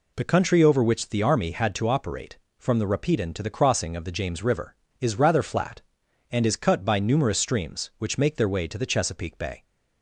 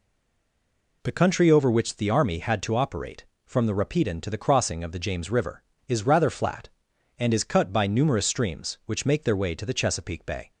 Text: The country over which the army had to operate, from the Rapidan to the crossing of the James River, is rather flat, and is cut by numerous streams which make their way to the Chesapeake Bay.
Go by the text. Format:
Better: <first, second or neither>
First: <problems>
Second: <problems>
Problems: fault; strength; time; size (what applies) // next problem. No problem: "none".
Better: first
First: none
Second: stays silent before the first word; until 1.0 s; 1.0 s long